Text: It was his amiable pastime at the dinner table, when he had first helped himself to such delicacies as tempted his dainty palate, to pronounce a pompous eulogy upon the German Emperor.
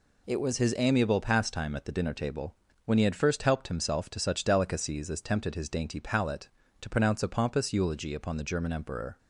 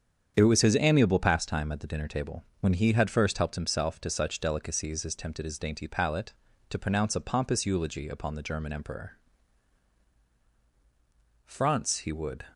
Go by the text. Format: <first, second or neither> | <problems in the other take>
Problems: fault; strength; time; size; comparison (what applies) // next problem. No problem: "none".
first | starts louder than the rest; strong; until 1.3 s; 8 dB // goes on to say "France he would"; noticeable; from 11.4 s on; 0.98 s long